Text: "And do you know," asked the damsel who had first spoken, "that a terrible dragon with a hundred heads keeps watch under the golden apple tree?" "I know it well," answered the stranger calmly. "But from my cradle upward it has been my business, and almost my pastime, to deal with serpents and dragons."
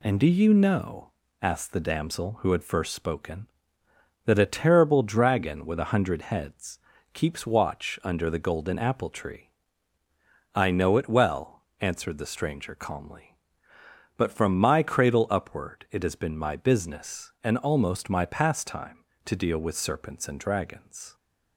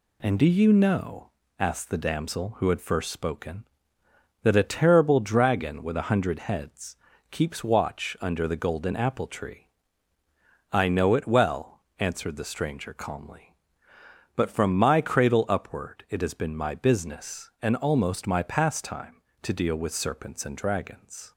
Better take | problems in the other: neither | pauses between "heads" and "keeps"; slight; the same in both

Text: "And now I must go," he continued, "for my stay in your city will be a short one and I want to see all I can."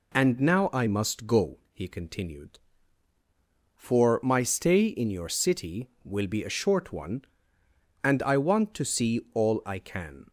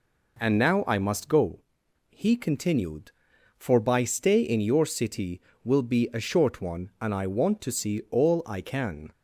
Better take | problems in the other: first | says "by" for "my"; at 3.8 s

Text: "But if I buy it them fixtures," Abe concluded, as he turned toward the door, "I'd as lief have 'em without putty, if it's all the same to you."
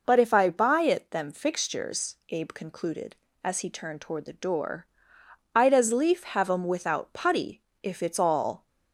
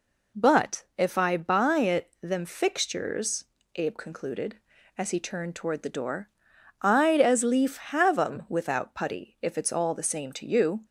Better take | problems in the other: second | stops before "the same to you"; at 8.6 s

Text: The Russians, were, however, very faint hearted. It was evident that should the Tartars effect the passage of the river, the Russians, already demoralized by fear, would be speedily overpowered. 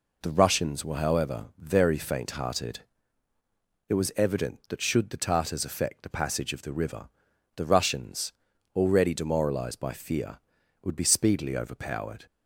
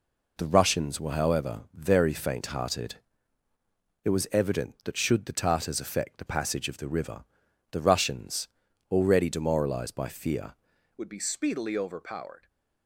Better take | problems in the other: first | changes voice at "would"; from 10.9 s on; 1.5 s long

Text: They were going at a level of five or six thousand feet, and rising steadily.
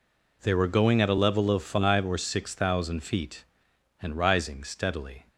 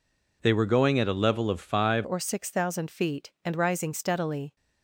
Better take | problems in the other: first | changes voice at "or"; from 2.0 s on; 2.5 s long

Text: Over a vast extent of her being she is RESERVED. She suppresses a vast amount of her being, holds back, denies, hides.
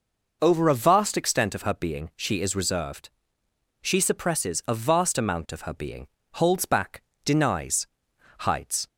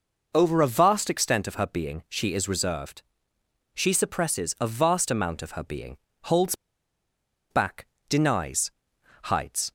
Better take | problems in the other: first | pauses between "holds" and "back"; noticeable; at 6.5 s; 0.97 s long

